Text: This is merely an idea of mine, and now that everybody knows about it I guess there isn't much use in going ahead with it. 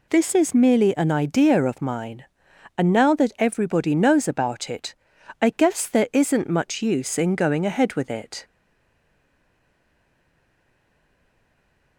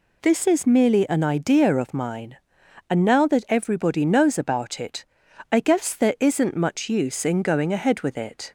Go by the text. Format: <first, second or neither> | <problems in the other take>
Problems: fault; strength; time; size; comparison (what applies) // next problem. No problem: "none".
second | pauses between "it" and "I"; noticeable; at 4.9 s; 0.48 s long; noticeable in the second // stays silent after the last word; strong; from 8.4 s on; 3.5 s long